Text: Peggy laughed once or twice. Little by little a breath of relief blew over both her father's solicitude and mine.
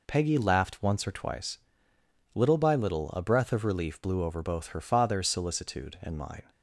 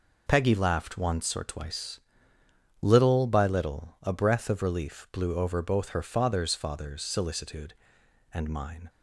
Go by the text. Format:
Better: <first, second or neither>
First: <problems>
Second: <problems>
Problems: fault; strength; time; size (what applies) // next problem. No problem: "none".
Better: first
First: none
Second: says "father's" twice; at 6.5 s